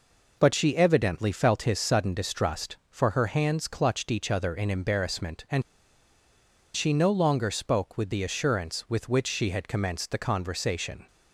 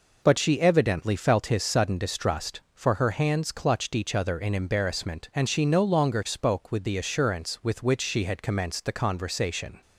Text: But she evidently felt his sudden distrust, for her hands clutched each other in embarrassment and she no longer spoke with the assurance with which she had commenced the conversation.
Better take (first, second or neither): second